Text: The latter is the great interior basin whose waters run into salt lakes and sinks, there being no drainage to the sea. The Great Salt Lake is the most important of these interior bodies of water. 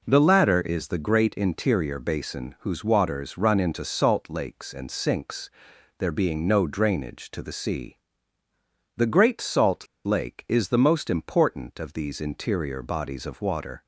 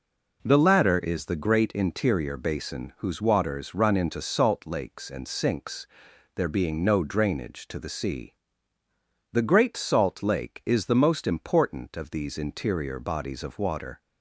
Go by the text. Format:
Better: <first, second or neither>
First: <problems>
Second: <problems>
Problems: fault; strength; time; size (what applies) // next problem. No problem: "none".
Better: second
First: pauses between "Salt" and "Lake"; slight; at 9.8 s; 0.18 s long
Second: none